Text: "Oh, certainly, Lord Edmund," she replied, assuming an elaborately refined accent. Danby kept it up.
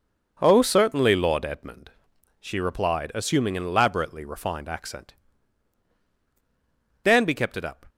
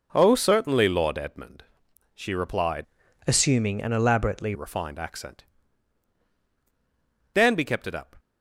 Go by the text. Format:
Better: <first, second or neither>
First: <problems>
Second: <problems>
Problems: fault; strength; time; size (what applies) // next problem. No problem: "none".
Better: first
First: none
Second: changes voice from "assuming" to "elaborately"; from 3.2 to 4.5 s; 1.3 s long